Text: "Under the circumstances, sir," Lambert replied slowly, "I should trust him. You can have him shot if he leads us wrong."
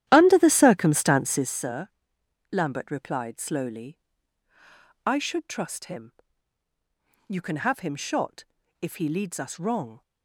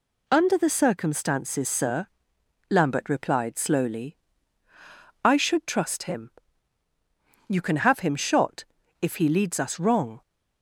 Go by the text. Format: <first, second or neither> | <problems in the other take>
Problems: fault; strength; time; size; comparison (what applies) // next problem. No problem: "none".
second | starts louder than the rest; strong; until 1.6 s; 12 dB // pauses between "shot" and "if"; at 8.4 s; 0.38 s long; also in the second